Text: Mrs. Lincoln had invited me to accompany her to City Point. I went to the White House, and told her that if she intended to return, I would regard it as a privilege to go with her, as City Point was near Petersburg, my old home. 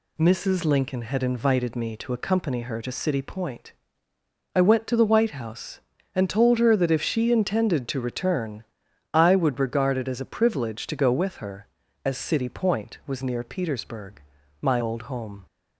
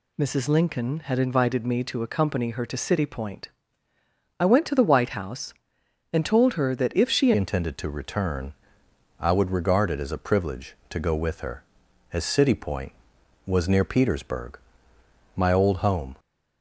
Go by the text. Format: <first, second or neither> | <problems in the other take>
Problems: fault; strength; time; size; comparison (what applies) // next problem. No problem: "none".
first | changes voice at "intended"; from 7.3 s on; 8.8 s long